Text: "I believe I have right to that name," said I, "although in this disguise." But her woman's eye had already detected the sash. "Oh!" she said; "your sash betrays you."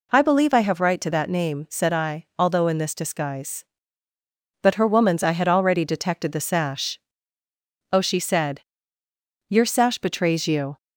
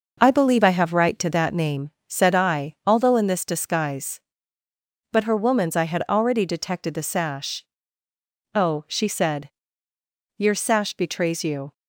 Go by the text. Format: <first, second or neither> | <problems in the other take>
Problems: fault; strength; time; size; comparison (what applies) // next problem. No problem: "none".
first | gets quieter; throughout; 6.5 dB